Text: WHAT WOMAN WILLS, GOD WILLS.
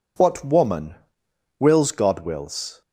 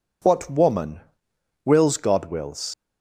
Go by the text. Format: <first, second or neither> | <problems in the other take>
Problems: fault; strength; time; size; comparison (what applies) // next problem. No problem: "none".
first | pauses between "WOMAN" and "WILLS"; noticeable; at 1.0 s; 0.64 s long; noticeable in the first // leaves "WILLS" unfinished; at 2.7 s; 130 ms